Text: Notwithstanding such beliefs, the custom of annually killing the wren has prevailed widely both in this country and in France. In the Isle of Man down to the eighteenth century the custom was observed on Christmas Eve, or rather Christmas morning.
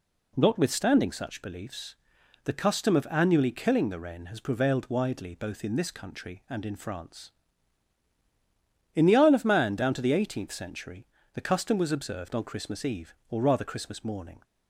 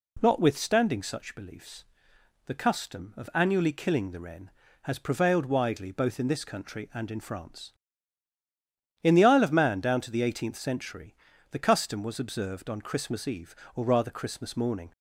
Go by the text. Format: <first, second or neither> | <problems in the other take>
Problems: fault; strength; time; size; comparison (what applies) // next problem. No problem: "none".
neither | pauses between "century" and "the"; the same in both